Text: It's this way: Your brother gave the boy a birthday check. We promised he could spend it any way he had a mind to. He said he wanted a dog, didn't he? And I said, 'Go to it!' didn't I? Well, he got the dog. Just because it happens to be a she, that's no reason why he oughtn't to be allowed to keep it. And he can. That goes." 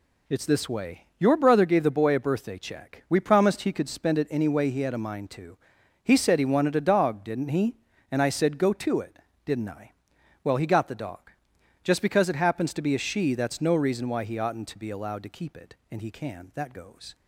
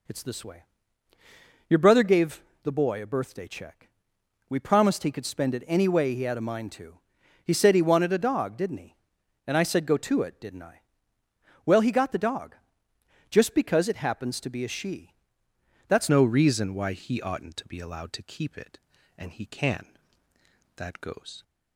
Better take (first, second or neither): first